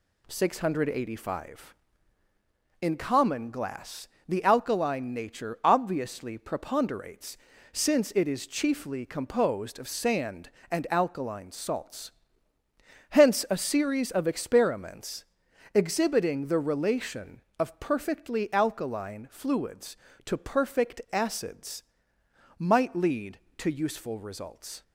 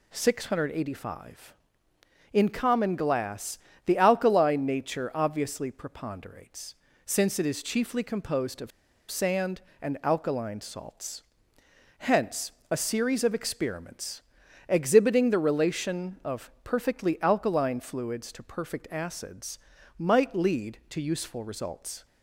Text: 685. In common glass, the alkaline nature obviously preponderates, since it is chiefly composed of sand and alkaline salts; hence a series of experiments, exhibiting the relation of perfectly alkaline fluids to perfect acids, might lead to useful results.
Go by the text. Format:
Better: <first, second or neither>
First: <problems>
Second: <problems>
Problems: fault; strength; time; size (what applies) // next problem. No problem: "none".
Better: first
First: none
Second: pauses between "of" and "sand"; at 8.7 s; 0.40 s long // pauses between "hence" and "a"; slight; at 12.5 s; 0.20 s long